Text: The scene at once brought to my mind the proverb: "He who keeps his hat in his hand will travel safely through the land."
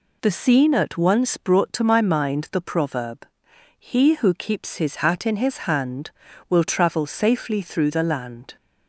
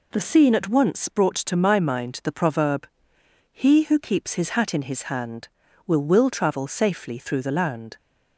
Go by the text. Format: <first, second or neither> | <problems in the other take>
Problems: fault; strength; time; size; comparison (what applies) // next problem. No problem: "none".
first | says "will" twice; at 6.0 s